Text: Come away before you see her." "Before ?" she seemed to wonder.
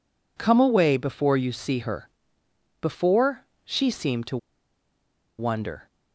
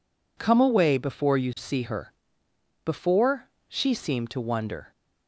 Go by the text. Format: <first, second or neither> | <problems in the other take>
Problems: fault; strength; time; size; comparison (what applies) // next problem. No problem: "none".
second | pauses between "to" and "wonder"; at 4.3 s; 1.0 s long